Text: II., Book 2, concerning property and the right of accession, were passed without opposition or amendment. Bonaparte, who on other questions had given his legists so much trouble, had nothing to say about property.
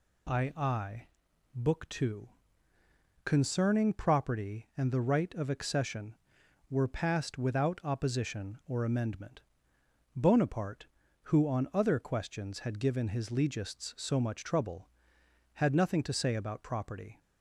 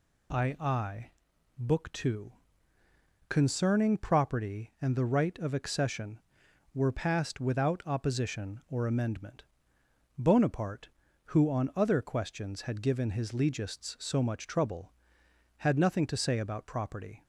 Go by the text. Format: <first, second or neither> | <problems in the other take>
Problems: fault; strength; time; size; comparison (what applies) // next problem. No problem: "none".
neither | none